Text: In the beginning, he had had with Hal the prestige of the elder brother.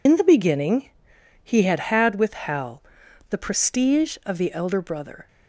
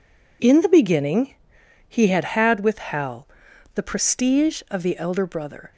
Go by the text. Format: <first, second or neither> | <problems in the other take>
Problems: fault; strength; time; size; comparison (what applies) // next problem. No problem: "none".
second | loses the start of "In"; at 0.0 s; 80 ms // pauses between "Hal" and "the"; noticeable; at 2.8 s; 0.46 s long; noticeable in the second